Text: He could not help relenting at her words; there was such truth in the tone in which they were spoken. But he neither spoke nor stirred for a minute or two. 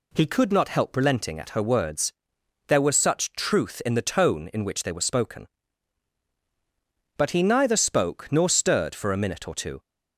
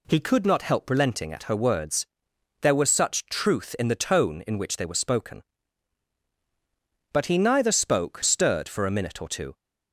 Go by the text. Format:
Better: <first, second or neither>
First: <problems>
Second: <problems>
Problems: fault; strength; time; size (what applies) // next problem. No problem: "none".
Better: first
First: none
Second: skips "nor"; at 8.2 s